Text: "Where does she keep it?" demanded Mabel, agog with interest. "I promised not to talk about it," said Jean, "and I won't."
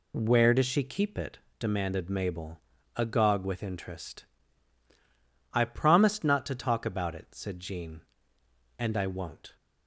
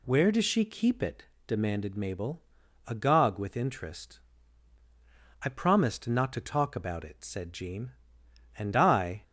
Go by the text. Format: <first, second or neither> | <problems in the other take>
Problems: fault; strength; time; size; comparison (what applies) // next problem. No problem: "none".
first | stops before "won't"; at 9.2 s